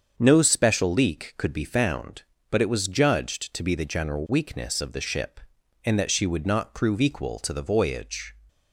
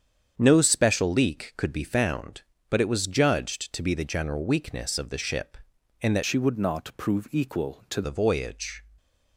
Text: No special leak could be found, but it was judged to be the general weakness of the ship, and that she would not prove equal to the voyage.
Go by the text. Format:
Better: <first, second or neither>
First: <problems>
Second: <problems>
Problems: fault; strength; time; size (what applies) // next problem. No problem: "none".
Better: first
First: starts louder than the rest; strong; until 1.1 s; 7 dB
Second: starts louder than the rest; strong; until 1.3 s; 8 dB // changes voice from "she" to "to"; from 6.2 to 8.0 s; 1.8 s long